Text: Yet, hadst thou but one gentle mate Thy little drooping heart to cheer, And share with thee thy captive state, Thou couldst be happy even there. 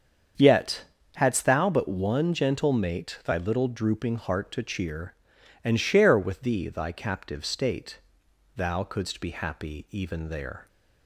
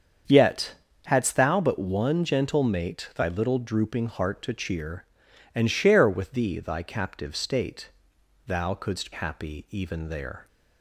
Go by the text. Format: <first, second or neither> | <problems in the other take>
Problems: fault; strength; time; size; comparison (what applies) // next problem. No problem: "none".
first | starts louder than the rest; strong; until 1.5 s; 7 dB; strong in the first // skips "be"; at 9.1 s